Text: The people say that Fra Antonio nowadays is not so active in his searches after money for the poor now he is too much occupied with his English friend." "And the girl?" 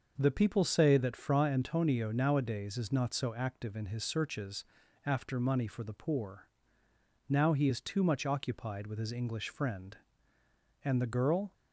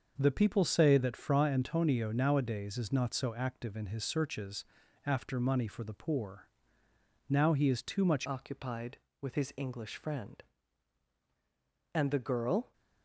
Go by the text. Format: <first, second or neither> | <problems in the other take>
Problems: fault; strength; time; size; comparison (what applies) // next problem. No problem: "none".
first | starts louder than the rest; until 1.1 s; 6 dB; also in the first // pauses between "searches" and "after"; at 4.6 s; 0.40 s long; also in the first // pauses between "poor" and "now"; noticeable; at 6.4 s; 0.80 s long; noticeable in the first // changes voice at "occupied"; from 8.2 s on; 4.5 s long